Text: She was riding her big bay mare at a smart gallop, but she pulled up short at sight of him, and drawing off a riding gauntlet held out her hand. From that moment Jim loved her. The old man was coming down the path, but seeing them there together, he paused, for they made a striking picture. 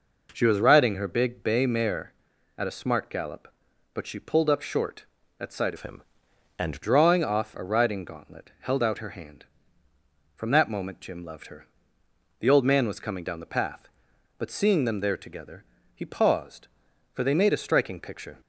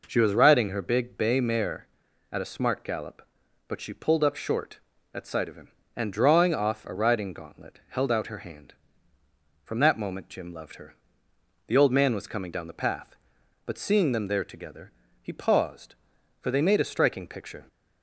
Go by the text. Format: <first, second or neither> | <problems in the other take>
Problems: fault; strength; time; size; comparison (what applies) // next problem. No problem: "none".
second | changes voice from "of" to "and"; from 5.7 to 6.8 s; 1.1 s long